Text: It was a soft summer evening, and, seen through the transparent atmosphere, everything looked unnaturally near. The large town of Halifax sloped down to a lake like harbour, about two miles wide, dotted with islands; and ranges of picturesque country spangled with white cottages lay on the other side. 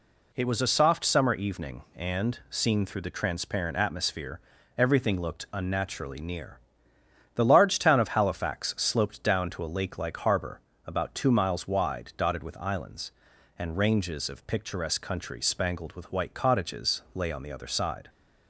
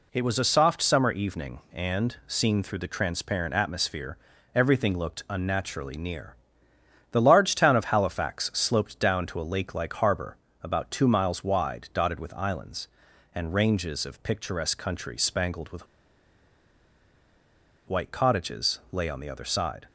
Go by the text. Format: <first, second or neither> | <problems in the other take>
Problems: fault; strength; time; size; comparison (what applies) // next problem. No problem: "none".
first | pauses between "with" and "white"; strong; at 15.8 s; 2.0 s long